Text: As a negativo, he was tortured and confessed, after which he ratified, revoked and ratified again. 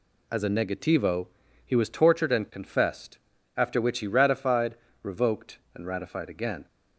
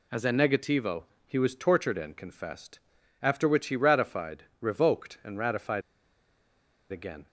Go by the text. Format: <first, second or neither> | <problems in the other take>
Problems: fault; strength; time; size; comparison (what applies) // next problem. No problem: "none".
first | pauses between "ratified" and "again"; at 5.8 s; 1.0 s long